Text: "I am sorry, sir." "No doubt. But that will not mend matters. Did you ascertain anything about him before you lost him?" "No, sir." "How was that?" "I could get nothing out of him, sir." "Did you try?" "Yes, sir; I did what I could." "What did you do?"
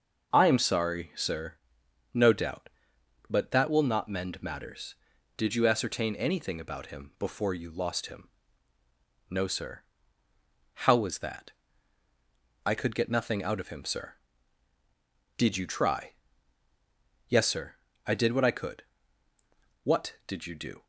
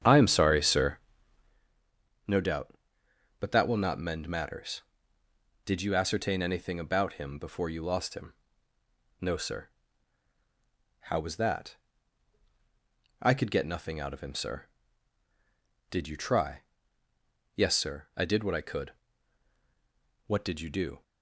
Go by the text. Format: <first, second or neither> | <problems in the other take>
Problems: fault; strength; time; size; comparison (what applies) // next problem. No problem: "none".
first | starts louder than the rest; strong; until 1.6 s; 8.5 dB